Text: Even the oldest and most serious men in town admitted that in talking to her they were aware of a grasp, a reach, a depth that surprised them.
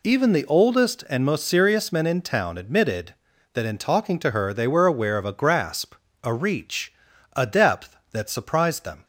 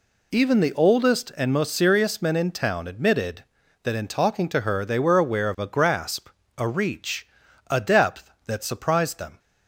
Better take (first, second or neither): neither